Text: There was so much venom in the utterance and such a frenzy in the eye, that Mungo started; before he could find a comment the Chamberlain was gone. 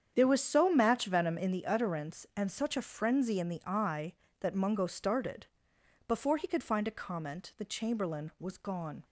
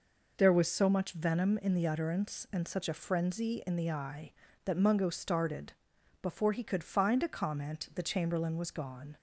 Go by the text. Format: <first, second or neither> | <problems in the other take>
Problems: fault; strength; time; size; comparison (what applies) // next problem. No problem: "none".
second | starts louder than the rest; strong; until 1.1 s; 8 dB // says "match" for "much"; at 0.7 s